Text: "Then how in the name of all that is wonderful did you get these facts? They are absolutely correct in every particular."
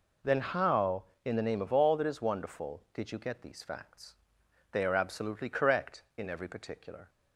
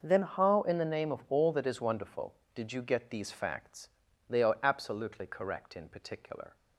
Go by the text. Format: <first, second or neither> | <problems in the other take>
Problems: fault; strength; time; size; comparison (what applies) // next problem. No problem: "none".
first | starts louder than the rest; noticeable; until 1.0 s; 6 dB // skips "every"; at 5.8 s